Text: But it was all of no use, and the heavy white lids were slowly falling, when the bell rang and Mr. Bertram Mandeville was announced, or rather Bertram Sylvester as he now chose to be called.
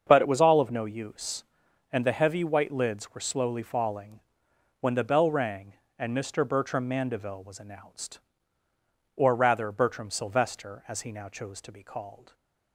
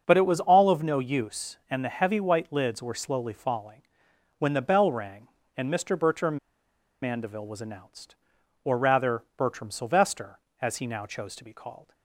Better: first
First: starts louder than the rest; until 1.0 s; 7 dB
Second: starts louder than the rest; until 1.0 s; 6.5 dB // pauses between "Bertram" and "Mandeville"; noticeable; at 6.3 s; 0.66 s long

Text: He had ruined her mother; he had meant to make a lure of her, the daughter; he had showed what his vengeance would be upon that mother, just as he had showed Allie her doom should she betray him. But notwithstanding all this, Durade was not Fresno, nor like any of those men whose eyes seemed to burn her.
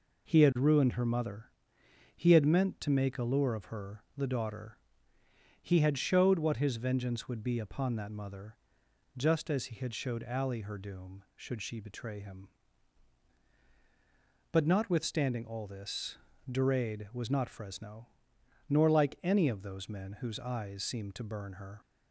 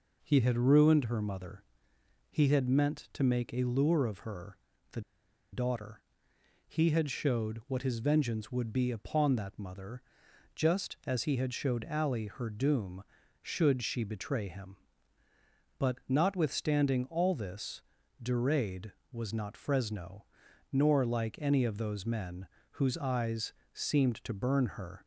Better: first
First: none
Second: pauses between "the" and "daughter"; noticeable; at 4.9 s; 0.52 s long // pauses between "men" and "whose"; slight; at 22.4 s; 0.26 s long // pauses between "eyes" and "seemed"; slight; at 23.5 s; 0.22 s long

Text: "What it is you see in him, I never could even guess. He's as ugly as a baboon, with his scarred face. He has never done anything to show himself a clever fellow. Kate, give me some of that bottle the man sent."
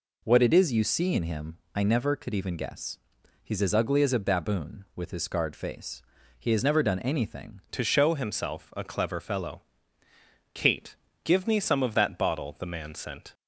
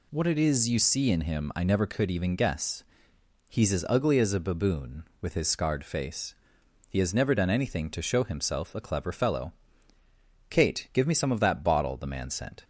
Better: second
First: changes voice at "to"; from 7.6 s on; 5.7 s long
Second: none

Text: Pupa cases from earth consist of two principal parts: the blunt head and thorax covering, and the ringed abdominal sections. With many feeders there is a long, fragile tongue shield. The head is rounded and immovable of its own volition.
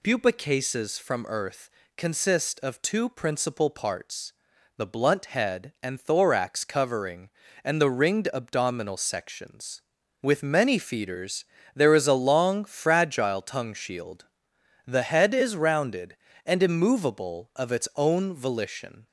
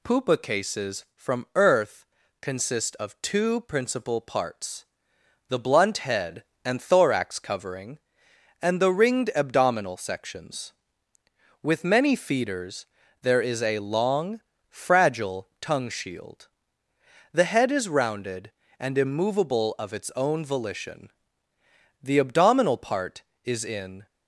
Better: first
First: pauses between "earth" and "consist"; slight; at 1.7 s; 0.26 s long // pauses between "feeders" and "there"; slight; at 11.4 s; 0.28 s long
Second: pauses between "earth" and "consist"; slight; at 2.0 s; 0.34 s long // pauses between "feeders" and "there"; slight; at 12.8 s; 0.36 s long // goes on to say "The abdominal part is in"; strong; from 22.0 s on; 2.0 s long

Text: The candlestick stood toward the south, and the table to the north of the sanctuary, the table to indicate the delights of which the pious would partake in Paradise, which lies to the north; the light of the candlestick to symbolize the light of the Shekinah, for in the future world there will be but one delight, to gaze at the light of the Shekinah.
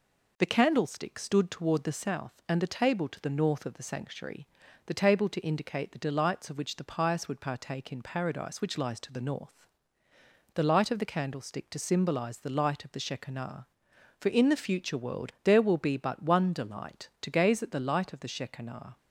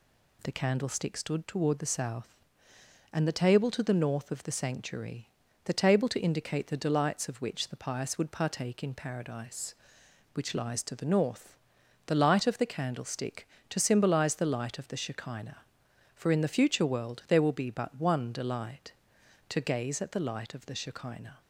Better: neither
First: none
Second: none

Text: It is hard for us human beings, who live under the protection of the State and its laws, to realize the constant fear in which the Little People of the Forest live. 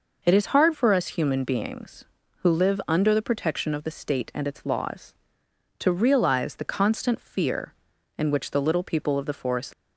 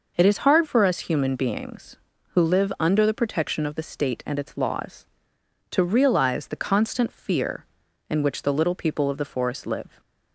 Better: second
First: stops before "live"; at 9.7 s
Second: none

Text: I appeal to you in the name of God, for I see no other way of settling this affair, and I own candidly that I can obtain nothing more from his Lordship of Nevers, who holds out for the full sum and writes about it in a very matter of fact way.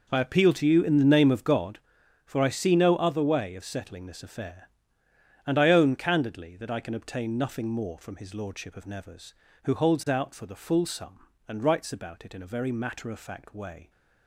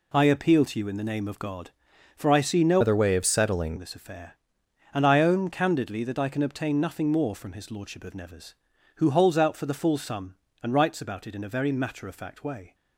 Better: first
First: none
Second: changes voice from "other" to "settling"; from 2.8 to 3.7 s; 0.9 s long

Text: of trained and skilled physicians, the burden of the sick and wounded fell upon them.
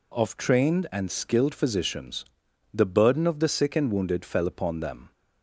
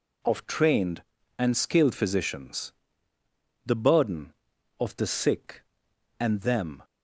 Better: first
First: none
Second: skips "wounded fell upon"; at 6.4 s

